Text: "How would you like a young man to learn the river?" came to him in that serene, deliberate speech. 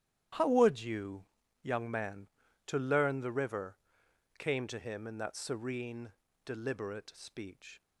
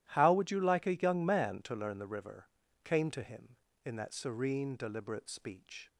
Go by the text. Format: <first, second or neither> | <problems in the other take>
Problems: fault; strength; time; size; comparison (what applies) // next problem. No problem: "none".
second | starts louder than the rest; strong; until 1.7 s; 11.5 dB; strong in the second // skips "like a"; at 1.4 s